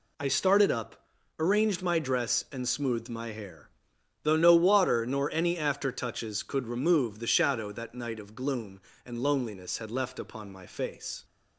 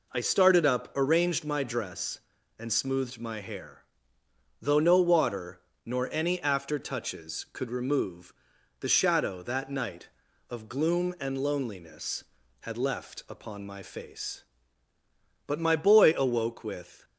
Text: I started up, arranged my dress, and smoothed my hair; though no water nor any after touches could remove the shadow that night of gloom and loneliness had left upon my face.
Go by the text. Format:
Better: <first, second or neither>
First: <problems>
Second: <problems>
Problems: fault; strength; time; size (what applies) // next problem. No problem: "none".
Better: first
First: none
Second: pauses between "water" and "nor"; slight; at 5.6 s; 0.24 s long // pauses between "remove" and "the"; noticeable; at 8.3 s; 0.48 s long // goes on to say "But my boy awoke with"; from 15.4 s on; 1.5 s long